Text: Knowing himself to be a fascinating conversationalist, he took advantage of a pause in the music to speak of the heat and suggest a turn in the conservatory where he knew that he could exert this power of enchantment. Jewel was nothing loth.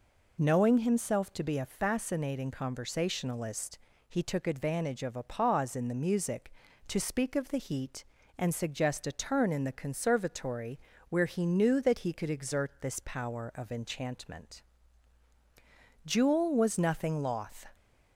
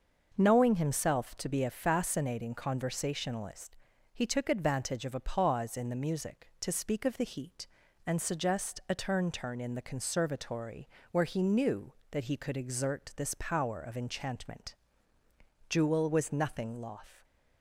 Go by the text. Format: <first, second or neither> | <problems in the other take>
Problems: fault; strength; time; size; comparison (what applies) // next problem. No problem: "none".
first | starts louder than the rest; until 1.3 s; 6 dB // says "turn" twice; at 9.3 s // pauses between "conservatory" and "where"; slight; at 10.8 s; 0.22 s long; slight in the first